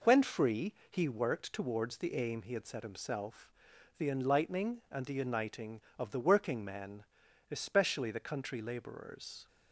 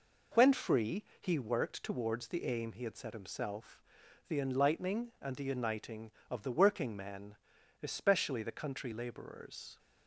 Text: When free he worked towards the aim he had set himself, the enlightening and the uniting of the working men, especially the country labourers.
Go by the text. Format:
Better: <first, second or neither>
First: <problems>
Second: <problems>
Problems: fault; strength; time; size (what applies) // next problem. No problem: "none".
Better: neither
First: pauses between "free" and "he"; slight; at 0.7 s; 0.16 s long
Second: pauses between "free" and "he"; slight; at 1.0 s; 0.16 s long